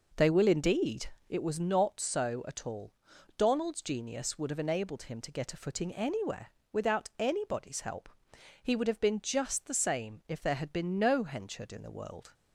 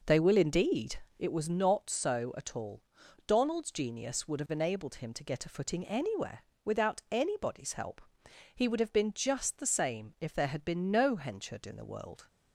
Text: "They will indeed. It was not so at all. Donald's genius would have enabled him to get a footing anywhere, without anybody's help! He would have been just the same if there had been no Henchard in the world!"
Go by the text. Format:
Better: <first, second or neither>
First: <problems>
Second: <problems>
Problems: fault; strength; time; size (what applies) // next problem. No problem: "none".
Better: neither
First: none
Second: none